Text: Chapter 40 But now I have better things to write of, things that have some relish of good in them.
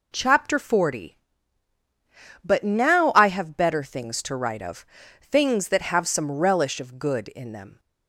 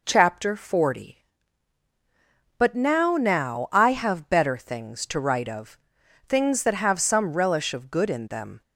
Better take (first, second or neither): first